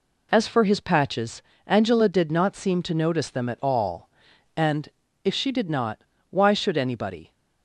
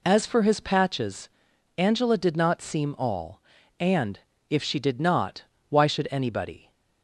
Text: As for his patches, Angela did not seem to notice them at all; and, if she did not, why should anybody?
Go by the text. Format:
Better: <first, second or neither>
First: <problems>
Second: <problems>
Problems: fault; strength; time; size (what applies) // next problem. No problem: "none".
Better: first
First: none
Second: skips "to notice them at"; at 2.9 s